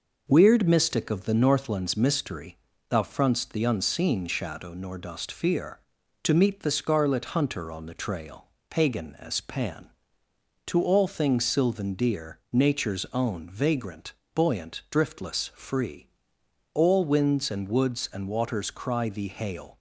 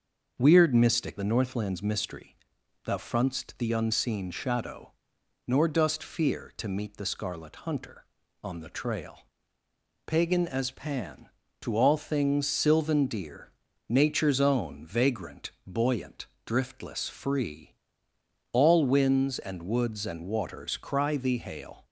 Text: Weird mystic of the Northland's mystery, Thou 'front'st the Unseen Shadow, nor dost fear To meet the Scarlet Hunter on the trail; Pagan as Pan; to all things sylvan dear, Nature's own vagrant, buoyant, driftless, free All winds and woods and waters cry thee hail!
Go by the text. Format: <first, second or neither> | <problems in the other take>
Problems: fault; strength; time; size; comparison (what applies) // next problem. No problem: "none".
first | starts louder than the rest; until 1.4 s; 6.5 dB // skips "of"; at 1.1 s // pauses between "free" and "All"; noticeable; at 17.7 s; 0.76 s long; noticeable in the first